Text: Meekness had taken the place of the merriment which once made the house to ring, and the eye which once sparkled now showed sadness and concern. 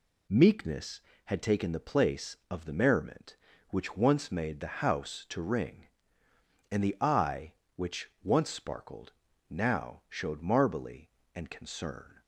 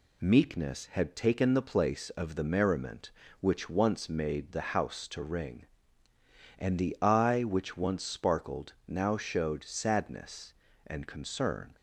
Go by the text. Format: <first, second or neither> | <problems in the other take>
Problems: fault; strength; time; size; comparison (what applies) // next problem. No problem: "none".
second | pauses between "sparkled" and "now"; at 9.1 s; 0.38 s long // says "marbly" for "sadness"; at 10.3 s